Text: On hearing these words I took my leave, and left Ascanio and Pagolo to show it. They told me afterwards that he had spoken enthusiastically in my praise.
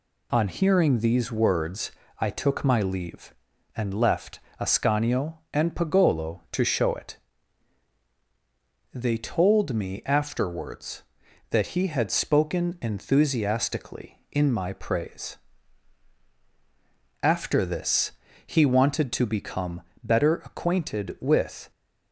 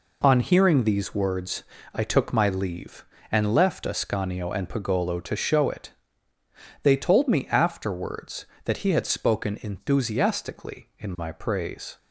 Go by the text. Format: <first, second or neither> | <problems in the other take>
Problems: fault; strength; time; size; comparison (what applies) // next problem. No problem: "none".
second | pauses between "words" and "I"; slight; at 1.9 s; 0.28 s long; slight in the second // pauses between "left" and "Ascanio"; slight; at 4.3 s; 0.20 s long // goes on to say "After this he wanted to become better acquainted with"; strong; from 17.2 s on; 4.4 s long